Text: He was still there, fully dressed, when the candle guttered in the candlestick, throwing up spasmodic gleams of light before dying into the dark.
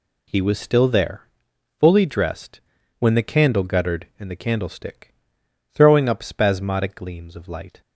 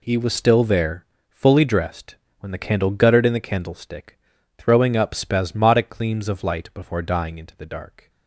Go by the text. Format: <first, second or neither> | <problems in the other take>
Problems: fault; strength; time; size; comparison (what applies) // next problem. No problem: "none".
second | stops before "before dying into the dark"; at 7.8 s